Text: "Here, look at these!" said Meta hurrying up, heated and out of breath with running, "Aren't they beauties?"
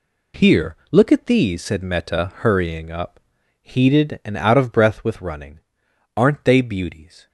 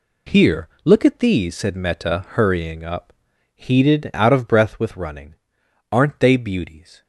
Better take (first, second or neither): first